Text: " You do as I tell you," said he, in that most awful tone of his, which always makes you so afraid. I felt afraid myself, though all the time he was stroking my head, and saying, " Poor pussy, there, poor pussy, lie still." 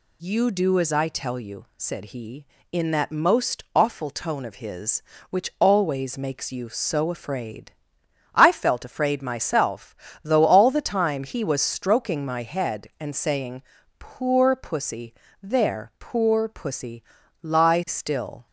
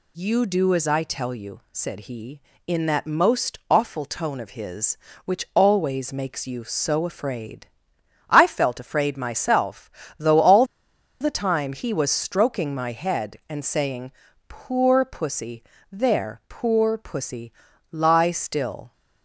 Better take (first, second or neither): first